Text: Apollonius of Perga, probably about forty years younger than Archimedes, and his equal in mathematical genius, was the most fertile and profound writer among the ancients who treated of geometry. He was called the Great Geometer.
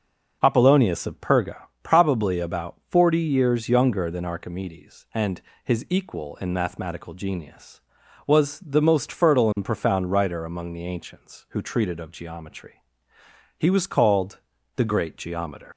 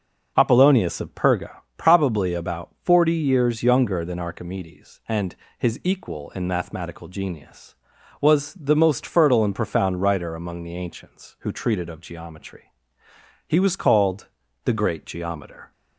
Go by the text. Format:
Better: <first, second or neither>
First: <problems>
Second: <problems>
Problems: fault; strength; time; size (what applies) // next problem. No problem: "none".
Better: second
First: pauses between "and" and "his"; slight; at 5.4 s; 0.24 s long // pauses between "called" and "the"; slight; at 14.4 s; 0.34 s long // leaves "Geometer" unfinished; at 15.7 s; 100 ms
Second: pauses between "and" and "his"; slight; at 5.3 s; 0.24 s long // pauses between "called" and "the"; slight; at 14.2 s; 0.34 s long